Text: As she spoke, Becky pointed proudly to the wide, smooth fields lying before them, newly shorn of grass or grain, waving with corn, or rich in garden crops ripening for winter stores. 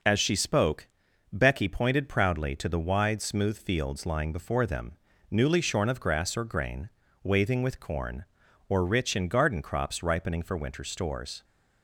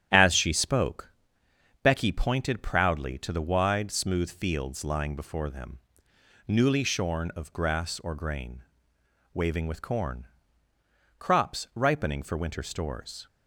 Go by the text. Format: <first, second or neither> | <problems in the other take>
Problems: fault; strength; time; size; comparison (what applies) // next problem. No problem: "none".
first | starts louder than the rest; strong; until 1.8 s; 10.5 dB // skips "or rich in garden"; at 10.7 s